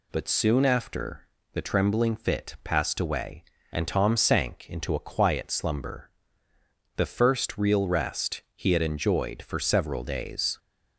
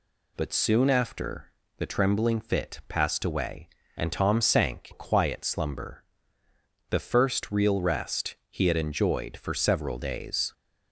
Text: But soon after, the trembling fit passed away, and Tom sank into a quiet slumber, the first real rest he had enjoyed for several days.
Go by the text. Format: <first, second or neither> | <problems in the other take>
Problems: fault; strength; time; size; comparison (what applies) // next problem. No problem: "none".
first | skips "into"; at 4.9 s